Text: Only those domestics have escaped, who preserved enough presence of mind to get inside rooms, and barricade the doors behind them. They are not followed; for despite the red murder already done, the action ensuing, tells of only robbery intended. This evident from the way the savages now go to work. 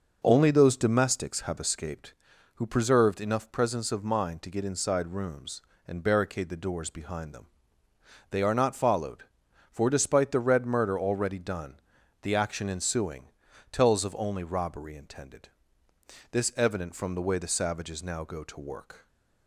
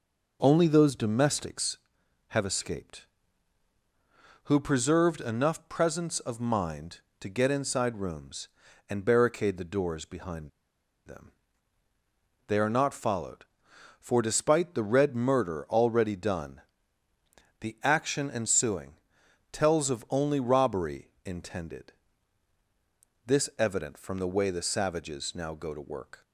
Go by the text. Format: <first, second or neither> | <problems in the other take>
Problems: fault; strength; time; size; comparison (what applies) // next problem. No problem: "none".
first | pauses between "behind" and "them"; noticeable; at 10.4 s; 0.56 s long